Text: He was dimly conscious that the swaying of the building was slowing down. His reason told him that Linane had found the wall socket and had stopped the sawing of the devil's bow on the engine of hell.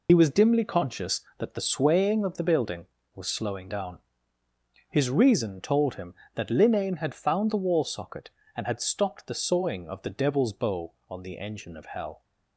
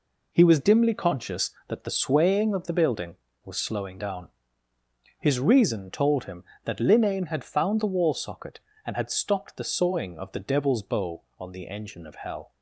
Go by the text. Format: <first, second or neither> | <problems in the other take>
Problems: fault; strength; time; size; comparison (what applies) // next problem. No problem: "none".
second | loses the start of "He"; at 0.0 s; 50 ms